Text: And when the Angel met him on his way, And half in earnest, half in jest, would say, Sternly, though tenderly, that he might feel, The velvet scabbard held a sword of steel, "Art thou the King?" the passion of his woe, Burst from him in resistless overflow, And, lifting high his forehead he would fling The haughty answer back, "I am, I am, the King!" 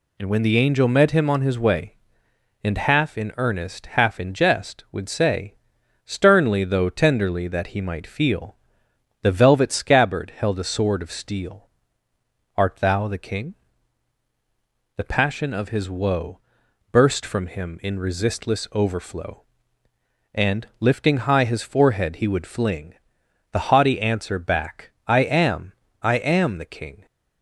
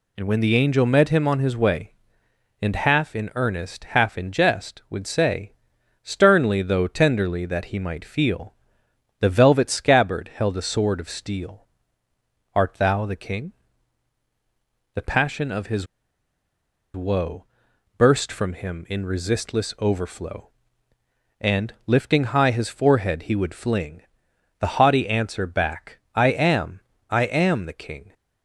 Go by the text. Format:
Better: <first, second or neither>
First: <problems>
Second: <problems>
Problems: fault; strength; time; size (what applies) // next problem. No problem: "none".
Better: first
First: pauses between "fling" and "The"; noticeable; at 22.9 s; 0.58 s long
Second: pauses between "his" and "woe"; at 15.8 s; 1.0 s long // pauses between "fling" and "The"; noticeable; at 24.0 s; 0.58 s long